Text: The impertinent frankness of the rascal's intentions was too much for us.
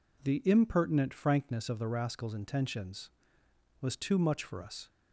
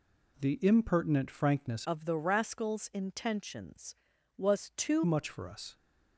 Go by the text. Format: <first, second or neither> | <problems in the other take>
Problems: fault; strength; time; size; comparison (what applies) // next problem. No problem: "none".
first | changes voice from "of" to "too"; from 1.8 to 5.0 s; 3.2 s long